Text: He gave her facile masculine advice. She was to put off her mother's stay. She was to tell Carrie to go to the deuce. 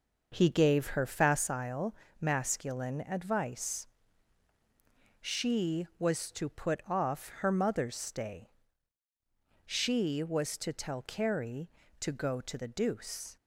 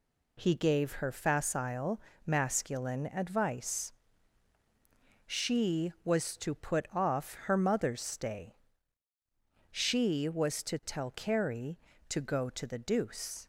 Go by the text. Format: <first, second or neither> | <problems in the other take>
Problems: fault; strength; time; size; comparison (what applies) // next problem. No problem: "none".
second | starts louder than the rest; noticeable; until 1.5 s; 6 dB // pauses between "facile" and "masculine"; slight; at 1.9 s; 0.24 s long; slight in the second